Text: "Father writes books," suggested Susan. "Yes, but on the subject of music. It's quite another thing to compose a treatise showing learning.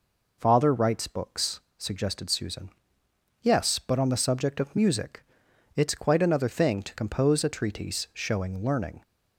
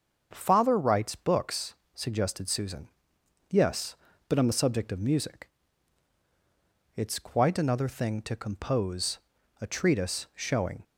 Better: first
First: none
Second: starts louder than the rest; until 1.3 s; 6.5 dB // pauses between "compose" and "a"; at 9.1 s; 0.42 s long // stops before "learning"; at 10.8 s

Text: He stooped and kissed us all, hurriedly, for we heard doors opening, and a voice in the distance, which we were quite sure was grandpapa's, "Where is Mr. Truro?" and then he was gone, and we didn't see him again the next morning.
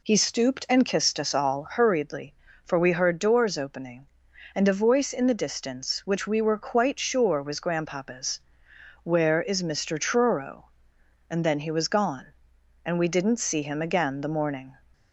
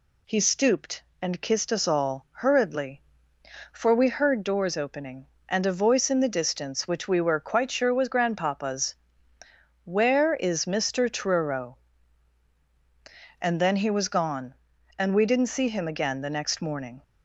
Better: second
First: skips "next"; at 14.2 s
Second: none

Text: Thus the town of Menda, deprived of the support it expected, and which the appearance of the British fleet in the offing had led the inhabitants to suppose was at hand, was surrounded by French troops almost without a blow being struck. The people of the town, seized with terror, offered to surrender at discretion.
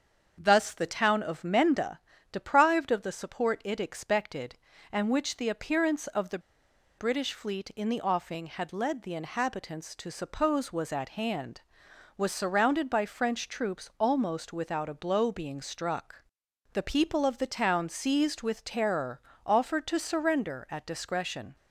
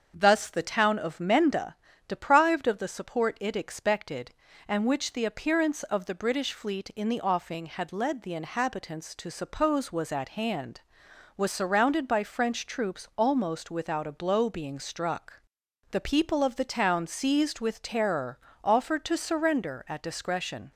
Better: second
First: starts louder than the rest; until 1.4 s; 7 dB // pauses between "the" and "British"; noticeable; at 6.3 s; 0.59 s long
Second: starts louder than the rest; until 1.1 s; 7 dB

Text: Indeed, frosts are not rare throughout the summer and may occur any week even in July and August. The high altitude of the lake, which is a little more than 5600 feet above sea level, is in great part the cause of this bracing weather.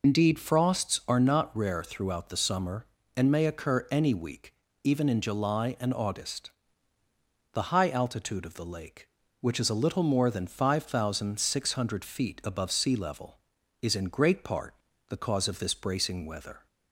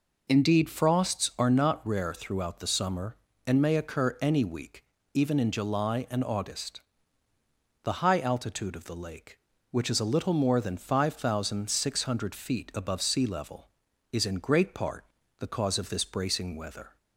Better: second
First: loses the start of "Indeed"; at 0.0 s; 55 ms // pauses between "week" and "even"; slight; at 4.5 s; 0.30 s long // pauses between "part" and "the"; slight; at 14.7 s; 0.34 s long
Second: pauses between "week" and "even"; slight; at 4.8 s; 0.30 s long // pauses between "part" and "the"; slight; at 15.0 s; 0.34 s long

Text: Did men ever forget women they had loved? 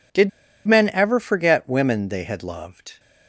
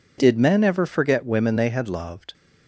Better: second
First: pauses between "Did" and "men"; at 0.2 s; 0.37 s long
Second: none

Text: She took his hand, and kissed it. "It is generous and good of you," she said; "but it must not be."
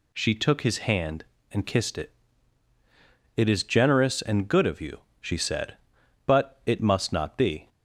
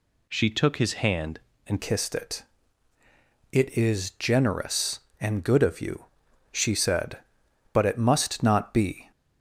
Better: first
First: none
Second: changes voice at "kissed"; from 1.8 s on; 7.3 s long

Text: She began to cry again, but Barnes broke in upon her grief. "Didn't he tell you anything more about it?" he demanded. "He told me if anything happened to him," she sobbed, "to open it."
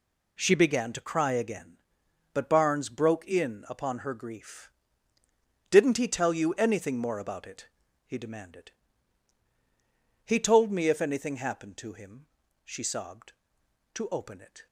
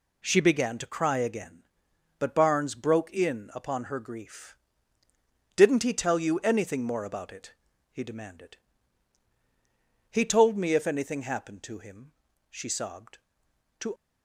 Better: first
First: none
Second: stops before "open it"; at 13.9 s

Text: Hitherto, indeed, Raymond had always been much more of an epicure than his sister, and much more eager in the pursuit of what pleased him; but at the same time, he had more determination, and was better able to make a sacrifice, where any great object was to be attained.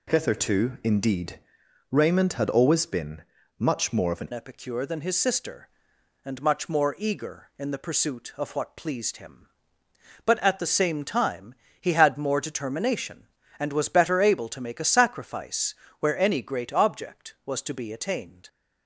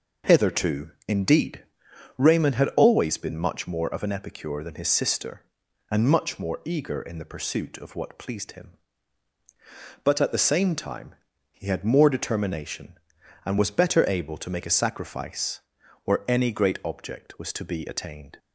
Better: second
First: pauses between "been" and "much"; at 3.2 s; 0.38 s long // changes voice at "epicure"; from 4.3 s on; 14.1 s long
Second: none

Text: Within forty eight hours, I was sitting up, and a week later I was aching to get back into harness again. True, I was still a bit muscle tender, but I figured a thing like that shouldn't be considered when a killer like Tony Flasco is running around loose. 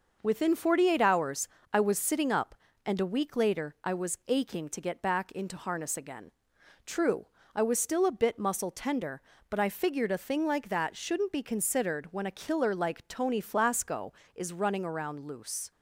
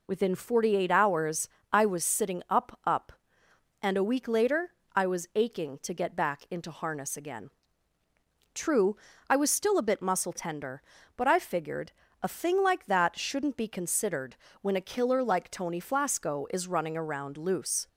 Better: first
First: none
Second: says "up" twice; at 2.8 s // pauses between "later" and "I"; slight; at 4.6 s; 0.24 s long // pauses between "figured" and "a"; slight; at 11.9 s; 0.30 s long // pauses between "considered" and "when"; slight; at 14.3 s; 0.26 s long

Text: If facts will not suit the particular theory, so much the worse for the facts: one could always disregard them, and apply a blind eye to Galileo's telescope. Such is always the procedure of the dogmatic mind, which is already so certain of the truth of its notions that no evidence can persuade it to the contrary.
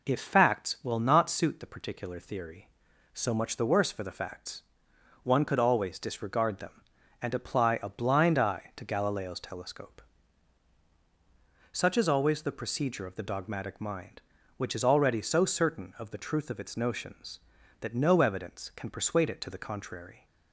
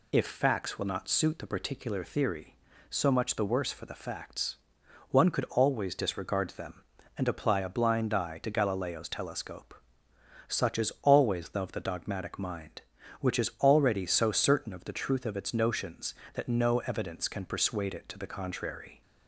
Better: first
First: none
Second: skips "procedure"; at 11.6 s

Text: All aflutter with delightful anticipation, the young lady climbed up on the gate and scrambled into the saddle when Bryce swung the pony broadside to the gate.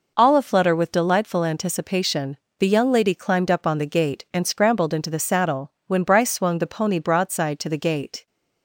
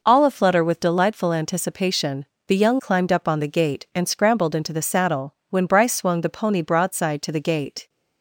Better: first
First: none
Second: skips "lady"; at 2.7 s

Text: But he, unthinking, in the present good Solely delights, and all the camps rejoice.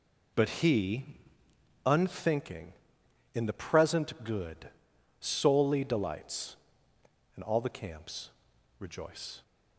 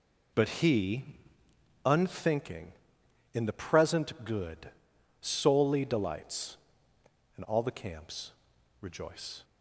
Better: neither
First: pauses between "good" and "Solely"; noticeable; at 4.6 s; 0.54 s long // pauses between "camps" and "rejoice"; noticeable; at 8.2 s; 0.50 s long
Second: pauses between "good" and "Solely"; noticeable; at 4.7 s; 0.54 s long // pauses between "camps" and "rejoice"; noticeable; at 8.3 s; 0.50 s long

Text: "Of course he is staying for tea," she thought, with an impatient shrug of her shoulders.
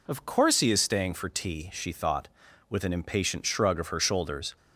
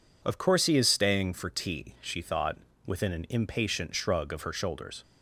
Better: first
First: none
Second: says "within" for "with"; at 2.8 s

